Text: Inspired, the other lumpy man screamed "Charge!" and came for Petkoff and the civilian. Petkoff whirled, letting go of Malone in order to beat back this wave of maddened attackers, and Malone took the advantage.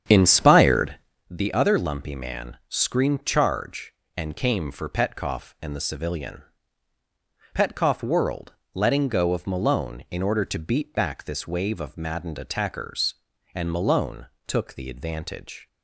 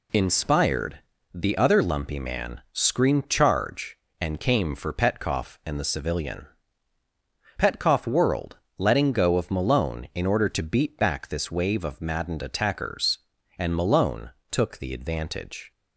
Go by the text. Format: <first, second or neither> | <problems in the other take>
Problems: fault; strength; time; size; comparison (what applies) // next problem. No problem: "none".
second | starts louder than the rest; strong; until 1.3 s; 9 dB // pauses between "Malone" and "took"; slight; at 14.2 s; 0.20 s long; slight in the second